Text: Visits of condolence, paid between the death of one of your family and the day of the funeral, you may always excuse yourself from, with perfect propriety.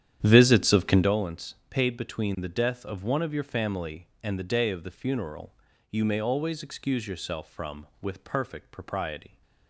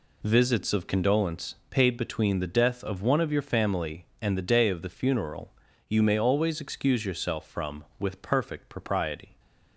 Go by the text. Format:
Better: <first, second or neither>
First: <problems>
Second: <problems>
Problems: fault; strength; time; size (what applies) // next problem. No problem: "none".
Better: second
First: starts louder than the rest; strong; until 1.1 s; 10 dB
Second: none